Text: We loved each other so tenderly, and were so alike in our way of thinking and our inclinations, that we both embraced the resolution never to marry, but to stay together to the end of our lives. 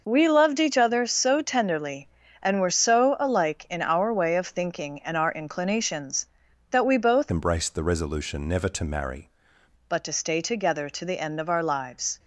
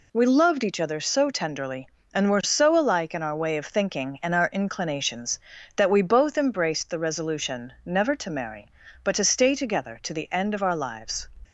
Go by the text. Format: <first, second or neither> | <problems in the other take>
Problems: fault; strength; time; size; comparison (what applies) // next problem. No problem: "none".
second | changes voice from "embraced" to "marry"; from 7.3 to 9.3 s; 2.0 s long